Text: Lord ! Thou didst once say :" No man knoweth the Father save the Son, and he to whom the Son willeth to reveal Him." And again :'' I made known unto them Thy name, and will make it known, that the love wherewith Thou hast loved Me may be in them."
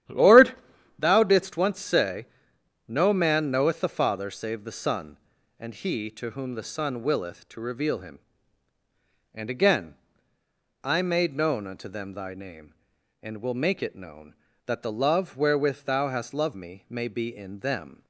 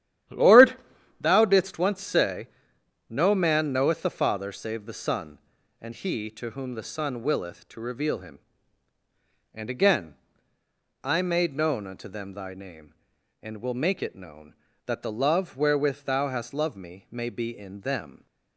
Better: neither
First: starts louder than the rest; strong; until 1.5 s; 12 dB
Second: starts louder than the rest; strong; until 1.7 s; 12 dB

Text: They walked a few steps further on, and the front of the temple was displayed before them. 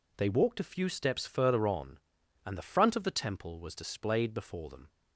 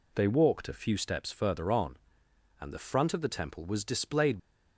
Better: first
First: none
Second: stops before "before them"; at 4.3 s

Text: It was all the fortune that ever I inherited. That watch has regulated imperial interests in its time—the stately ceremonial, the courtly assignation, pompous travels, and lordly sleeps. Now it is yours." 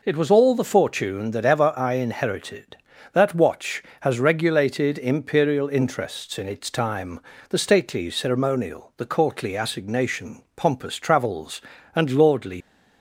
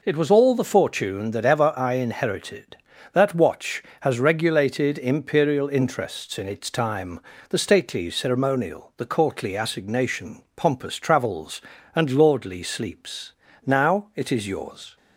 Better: second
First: stops before "sleeps Now it is yours"; at 12.6 s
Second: none

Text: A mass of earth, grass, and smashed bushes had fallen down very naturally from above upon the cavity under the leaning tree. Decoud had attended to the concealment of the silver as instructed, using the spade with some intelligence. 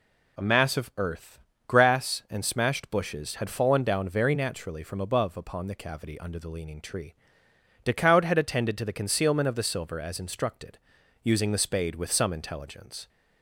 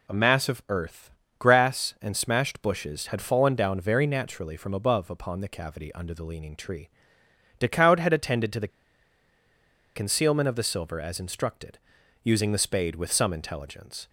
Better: first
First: none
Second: pauses between "the" and "concealment"; strong; at 8.6 s; 1.2 s long

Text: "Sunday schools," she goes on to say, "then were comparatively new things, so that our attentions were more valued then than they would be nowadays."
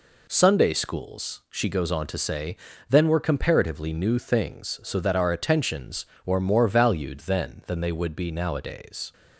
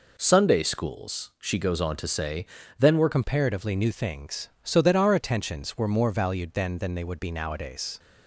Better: first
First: none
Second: changes voice at "comparatively"; from 3.1 s on; 4.8 s long

